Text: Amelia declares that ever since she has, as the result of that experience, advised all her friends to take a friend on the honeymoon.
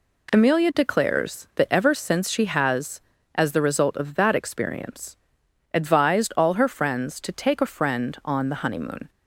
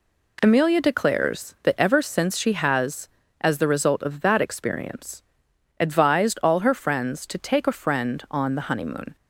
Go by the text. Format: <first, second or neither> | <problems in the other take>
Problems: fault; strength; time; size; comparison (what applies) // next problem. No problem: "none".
neither | none